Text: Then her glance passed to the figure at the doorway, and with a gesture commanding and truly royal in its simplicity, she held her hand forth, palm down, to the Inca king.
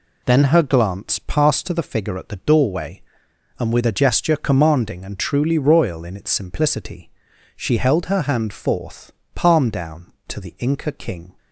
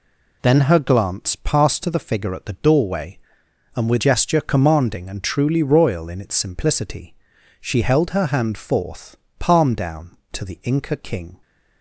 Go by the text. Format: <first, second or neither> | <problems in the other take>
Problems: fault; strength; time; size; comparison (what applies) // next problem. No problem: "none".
first | skips "a"; at 3.9 s